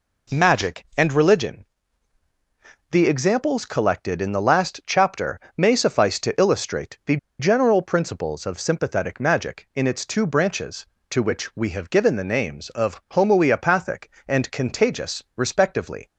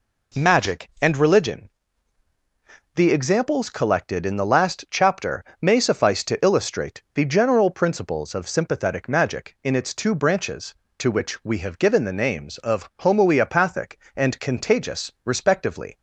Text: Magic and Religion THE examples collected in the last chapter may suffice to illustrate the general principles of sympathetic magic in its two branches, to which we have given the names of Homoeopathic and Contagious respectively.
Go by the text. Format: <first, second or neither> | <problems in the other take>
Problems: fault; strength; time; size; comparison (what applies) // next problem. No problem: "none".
second | pauses between "Religion" and "THE"; strong; at 1.6 s; 1.2 s long; strong in the second // pauses between "chapter" and "may"; slight; at 5.4 s; 0.16 s long; slight in the second // pauses between "the" and "general"; slight; at 7.1 s; 0.23 s long